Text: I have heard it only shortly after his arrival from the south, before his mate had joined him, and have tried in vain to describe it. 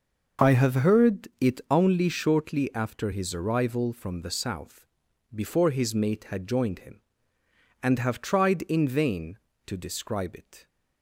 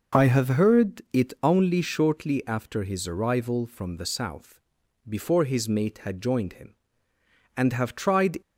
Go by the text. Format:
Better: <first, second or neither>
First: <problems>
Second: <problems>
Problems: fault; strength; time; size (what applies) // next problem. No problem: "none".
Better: first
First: none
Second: stops before "in vain to describe it"; at 8.4 s